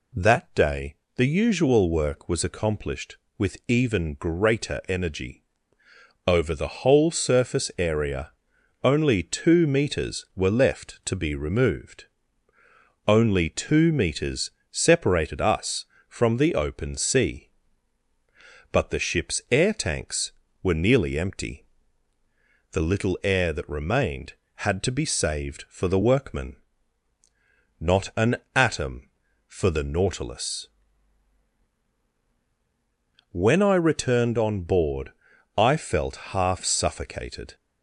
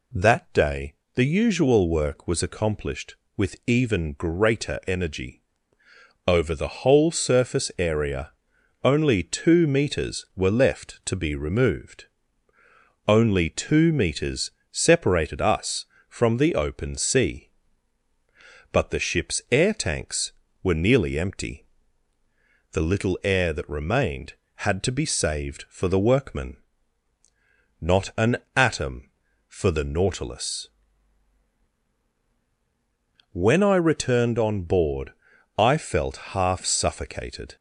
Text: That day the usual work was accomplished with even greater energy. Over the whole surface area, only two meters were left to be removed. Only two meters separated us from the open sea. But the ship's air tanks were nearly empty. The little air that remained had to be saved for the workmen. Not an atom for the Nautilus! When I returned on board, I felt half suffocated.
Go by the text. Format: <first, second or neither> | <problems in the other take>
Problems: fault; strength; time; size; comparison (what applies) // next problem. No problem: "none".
neither | pauses between "day" and "the"; slight; the same in both // pauses between "meters" and "separated"; slight; the same in both // pauses between "an" and "atom"; slight; the same in both // pauses between "felt" and "half"; slight; the same in both